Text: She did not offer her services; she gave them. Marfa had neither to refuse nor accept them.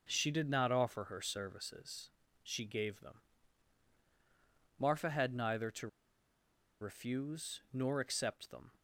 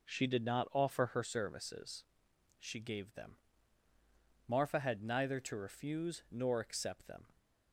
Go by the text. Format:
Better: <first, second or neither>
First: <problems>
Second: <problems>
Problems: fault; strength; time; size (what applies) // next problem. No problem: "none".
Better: second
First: pauses between "to" and "refuse"; noticeable; at 5.8 s; 0.93 s long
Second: none